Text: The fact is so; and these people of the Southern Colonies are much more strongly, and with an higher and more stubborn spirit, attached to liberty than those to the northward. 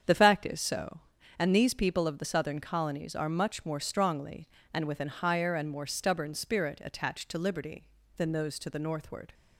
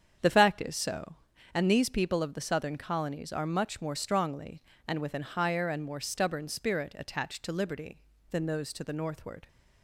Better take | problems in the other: neither | starts louder than the rest; strong; the same in both

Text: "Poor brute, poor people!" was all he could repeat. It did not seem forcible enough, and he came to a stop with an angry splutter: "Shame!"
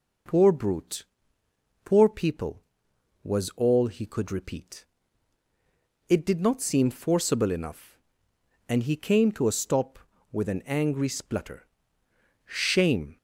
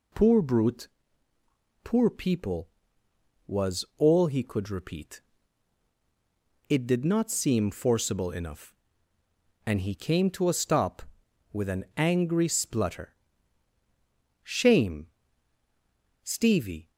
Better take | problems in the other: first | goes on to say "Stevie"; noticeable; from 16.2 s on; 0.66 s long

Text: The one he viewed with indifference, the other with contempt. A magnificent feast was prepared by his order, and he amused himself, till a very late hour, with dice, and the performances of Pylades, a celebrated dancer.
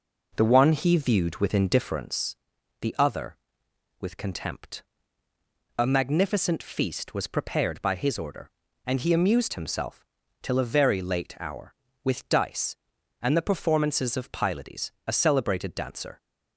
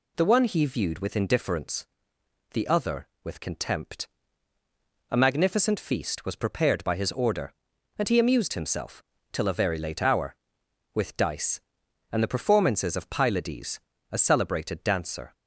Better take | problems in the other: second | starts louder than the rest; noticeable; until 2.1 s; 4.5 dB

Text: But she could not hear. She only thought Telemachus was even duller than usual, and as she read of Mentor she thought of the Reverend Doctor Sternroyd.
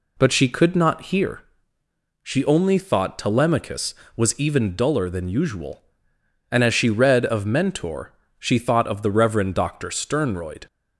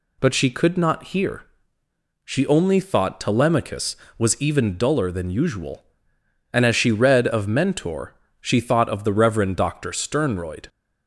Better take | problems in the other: second | starts louder than the rest; slight; until 1.4 s; 2.5 dB // pauses between "Mentor" and "she"; slight; at 8.1 s; 0.26 s long; slight in the second

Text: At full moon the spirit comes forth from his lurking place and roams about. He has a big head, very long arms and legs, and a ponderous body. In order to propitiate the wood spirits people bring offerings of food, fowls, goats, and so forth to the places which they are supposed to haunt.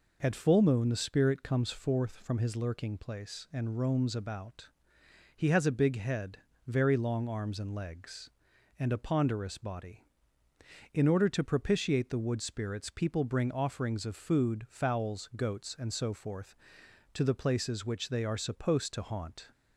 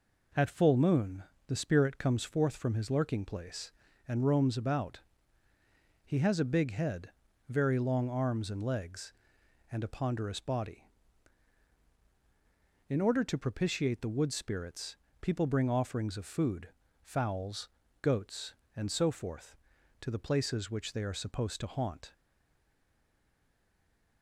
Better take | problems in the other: first | pauses between "moon" and "the"; slight; at 1.2 s; 0.24 s long // pauses between "spirits" and "people"; slight; at 14.9 s; 0.24 s long // stays silent after the last word; from 22.1 s on; 2.1 s long

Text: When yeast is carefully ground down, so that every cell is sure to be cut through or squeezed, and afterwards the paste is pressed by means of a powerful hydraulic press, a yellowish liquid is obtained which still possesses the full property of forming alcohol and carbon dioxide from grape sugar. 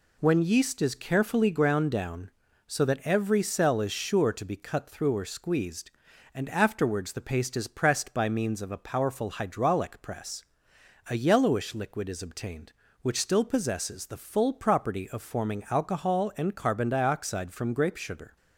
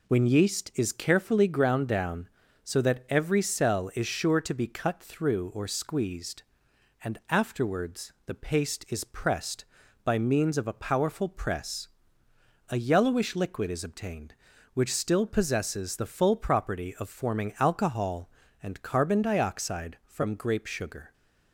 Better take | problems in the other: first | skips "hydraulic"; at 11.2 s

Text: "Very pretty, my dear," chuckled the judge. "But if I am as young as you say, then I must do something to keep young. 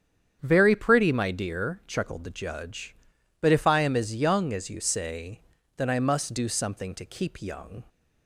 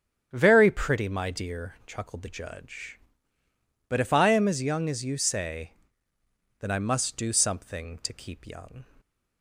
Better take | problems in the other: neither | starts louder than the rest; strong; the same in both

